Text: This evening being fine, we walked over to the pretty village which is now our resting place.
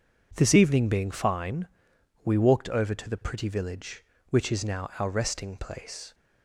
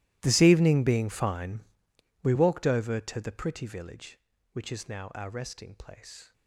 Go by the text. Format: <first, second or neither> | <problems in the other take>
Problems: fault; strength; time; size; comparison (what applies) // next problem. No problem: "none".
first | gets quieter; strong; throughout; 22 dB